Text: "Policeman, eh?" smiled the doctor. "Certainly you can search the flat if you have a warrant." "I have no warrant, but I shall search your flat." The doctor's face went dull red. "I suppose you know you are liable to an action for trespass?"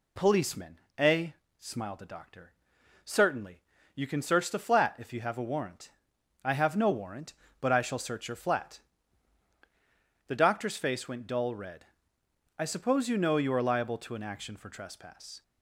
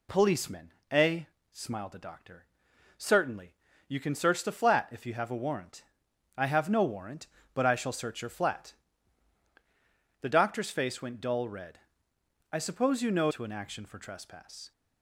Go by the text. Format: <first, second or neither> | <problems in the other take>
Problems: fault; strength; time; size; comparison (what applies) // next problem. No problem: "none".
first | pauses between "Certainly" and "you"; slight; at 3.5 s; 0.32 s long; slight in the first // skips "you are liable"; at 13.3 s